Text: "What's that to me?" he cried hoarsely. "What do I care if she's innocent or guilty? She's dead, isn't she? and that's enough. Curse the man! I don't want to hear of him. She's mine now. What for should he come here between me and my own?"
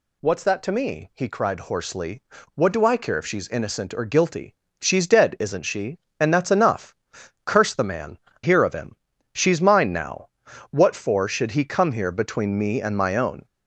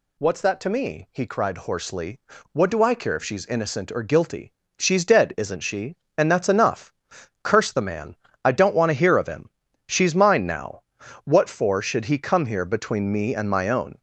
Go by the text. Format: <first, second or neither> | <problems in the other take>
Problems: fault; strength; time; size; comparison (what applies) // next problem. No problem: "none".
second | skips "I don't want to"; at 8.3 s